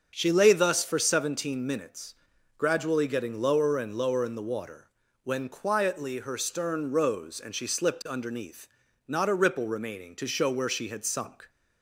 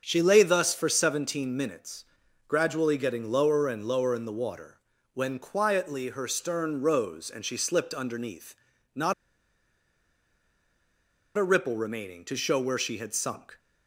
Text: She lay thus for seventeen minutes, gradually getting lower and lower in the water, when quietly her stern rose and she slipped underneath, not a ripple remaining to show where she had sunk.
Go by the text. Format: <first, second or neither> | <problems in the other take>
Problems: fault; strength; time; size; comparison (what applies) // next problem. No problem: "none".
first | starts louder than the rest; until 1.0 s; 7 dB; also in the first // pauses between "not" and "a"; strong; at 9.1 s; 2.2 s long